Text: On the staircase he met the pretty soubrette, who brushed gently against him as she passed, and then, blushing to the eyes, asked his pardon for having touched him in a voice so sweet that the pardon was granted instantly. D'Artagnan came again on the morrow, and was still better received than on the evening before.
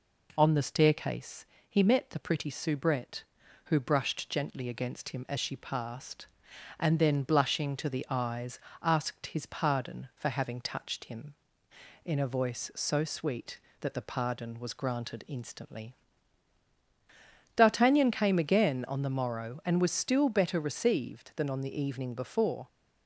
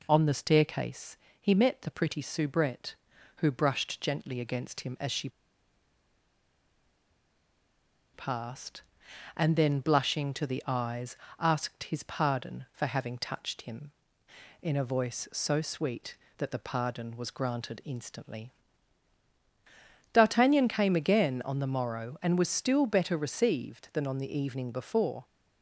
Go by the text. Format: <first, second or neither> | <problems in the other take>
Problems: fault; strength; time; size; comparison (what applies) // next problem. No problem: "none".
first | pauses between "staircase" and "he"; slight; at 1.1 s; 0.24 s long; slight in the first // pauses between "she" and "passed"; strong; at 5.2 s; 2.8 s long